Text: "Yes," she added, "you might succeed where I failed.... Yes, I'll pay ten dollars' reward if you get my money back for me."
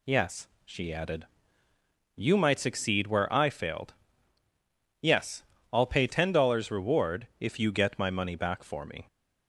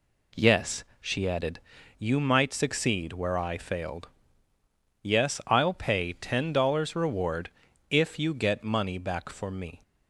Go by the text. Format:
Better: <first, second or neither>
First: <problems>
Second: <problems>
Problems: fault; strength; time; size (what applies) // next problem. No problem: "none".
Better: first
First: none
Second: pauses between "reward" and "if"; at 7.4 s; 0.42 s long // skips "my"; at 8.6 s